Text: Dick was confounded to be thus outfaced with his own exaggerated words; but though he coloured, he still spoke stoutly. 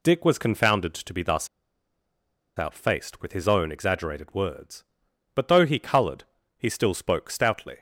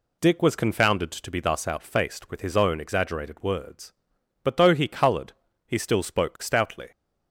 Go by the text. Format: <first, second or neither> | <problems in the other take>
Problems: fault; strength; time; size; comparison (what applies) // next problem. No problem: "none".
second | pauses between "thus" and "outfaced"; at 1.4 s; 1.0 s long